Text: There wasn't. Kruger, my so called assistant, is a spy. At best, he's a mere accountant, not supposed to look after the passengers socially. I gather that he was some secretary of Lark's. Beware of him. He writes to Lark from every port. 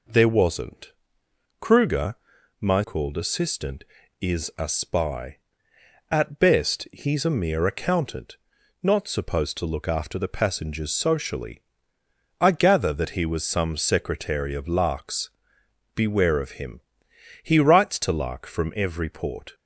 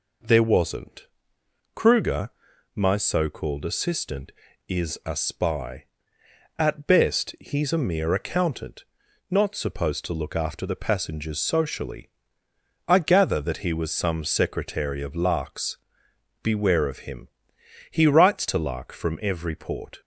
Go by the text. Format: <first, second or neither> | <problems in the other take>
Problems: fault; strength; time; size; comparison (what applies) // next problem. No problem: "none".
second | skips "so"; at 2.8 s